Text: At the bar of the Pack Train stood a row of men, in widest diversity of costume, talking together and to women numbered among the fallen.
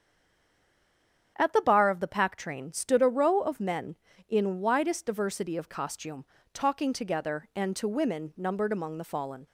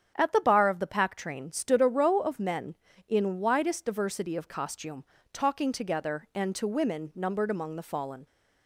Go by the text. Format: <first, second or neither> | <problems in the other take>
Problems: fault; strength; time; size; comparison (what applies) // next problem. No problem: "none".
second | stays silent before the first word; noticeable; until 1.3 s; 1.3 s long // starts louder than the rest; strong; until 2.3 s; 8 dB; strong in the second